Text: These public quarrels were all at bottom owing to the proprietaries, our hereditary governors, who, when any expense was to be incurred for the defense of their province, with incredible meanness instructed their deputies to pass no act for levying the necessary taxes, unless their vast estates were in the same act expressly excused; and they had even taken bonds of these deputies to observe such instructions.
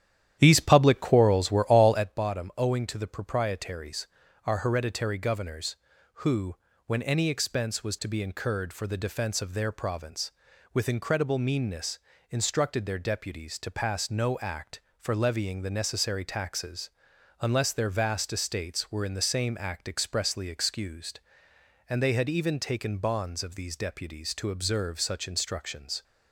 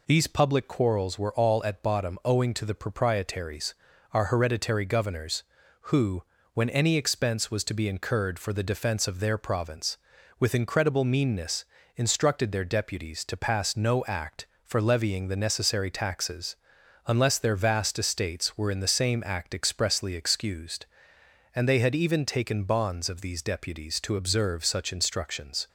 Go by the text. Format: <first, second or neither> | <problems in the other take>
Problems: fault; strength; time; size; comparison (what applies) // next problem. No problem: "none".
second | starts louder than the rest; strong; until 2.1 s; 11 dB // pauses between "meanness" and "instructed"; slight; at 11.9 s; 0.30 s long; slight in the second